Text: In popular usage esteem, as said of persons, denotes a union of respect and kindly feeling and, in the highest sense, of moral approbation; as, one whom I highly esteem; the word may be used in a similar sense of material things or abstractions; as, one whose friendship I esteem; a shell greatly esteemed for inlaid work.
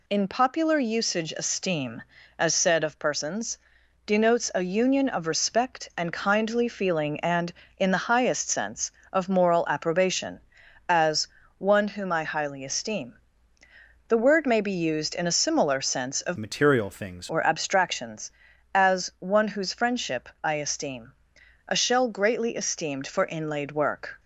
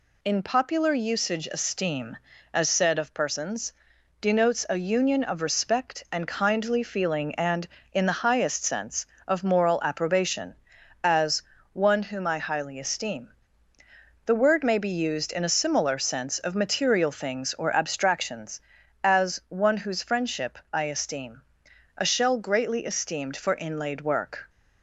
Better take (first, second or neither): second